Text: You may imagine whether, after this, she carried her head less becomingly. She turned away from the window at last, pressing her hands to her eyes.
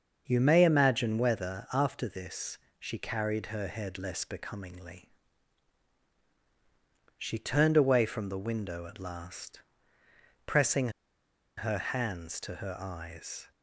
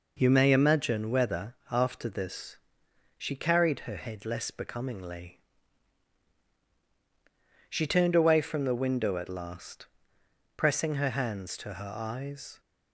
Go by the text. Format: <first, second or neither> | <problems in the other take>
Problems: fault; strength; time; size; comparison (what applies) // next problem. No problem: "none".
second | starts louder than the rest; until 1.2 s; 6.5 dB // pauses between "pressing" and "her"; noticeable; at 10.8 s; 0.68 s long